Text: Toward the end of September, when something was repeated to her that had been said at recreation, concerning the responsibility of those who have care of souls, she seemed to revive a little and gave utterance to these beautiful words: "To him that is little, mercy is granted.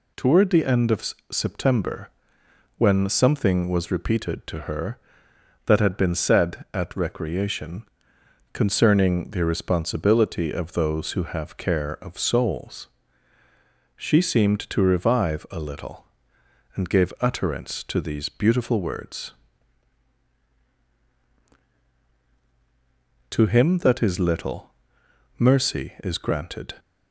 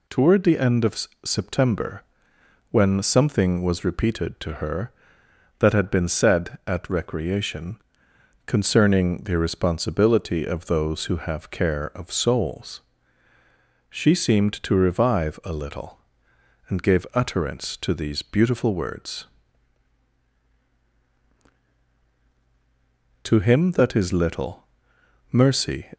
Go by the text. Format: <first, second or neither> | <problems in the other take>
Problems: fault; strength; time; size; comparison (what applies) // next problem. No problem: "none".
first | pauses between "of" and "September"; slight; at 1.0 s; 0.18 s long; slight in the first // stops before "is granted"; at 25.9 s